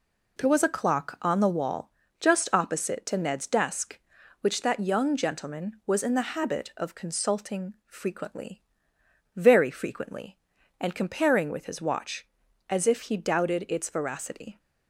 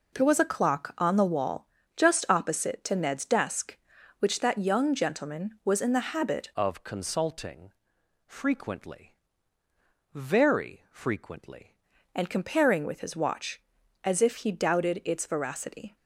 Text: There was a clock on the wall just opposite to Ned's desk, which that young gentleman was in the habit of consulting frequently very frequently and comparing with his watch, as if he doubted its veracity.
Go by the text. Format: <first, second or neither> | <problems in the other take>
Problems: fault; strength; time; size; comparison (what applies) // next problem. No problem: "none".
first | pauses between "wall" and "just"; slight; at 1.6 s; 0.30 s long; slight in the first // changes voice from "of" to "frequently"; from 6.5 to 11.7 s; 5.2 s long // pauses between "consulting" and "frequently"; noticeable; at 7.7 s; 0.54 s long // pauses between "frequently" and "very"; noticeable; at 9.1 s; 0.98 s long; noticeable in the first